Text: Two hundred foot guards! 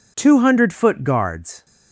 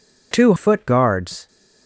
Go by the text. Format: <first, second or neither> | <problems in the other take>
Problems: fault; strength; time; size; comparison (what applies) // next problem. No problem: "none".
first | skips "hundred"; at 0.5 s